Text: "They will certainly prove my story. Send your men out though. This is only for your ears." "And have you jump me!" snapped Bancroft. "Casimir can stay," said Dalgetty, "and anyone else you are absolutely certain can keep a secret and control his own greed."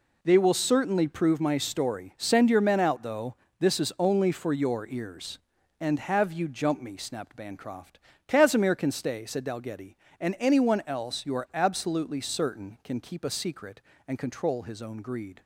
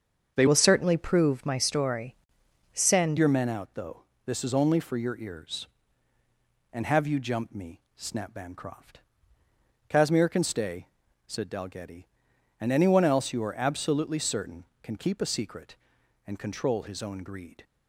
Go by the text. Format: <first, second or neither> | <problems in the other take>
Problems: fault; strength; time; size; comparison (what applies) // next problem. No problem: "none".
first | starts louder than the rest; until 1.3 s; 7 dB // changes voice from "will" to "Send"; from 0.4 to 3.1 s; 2.7 s long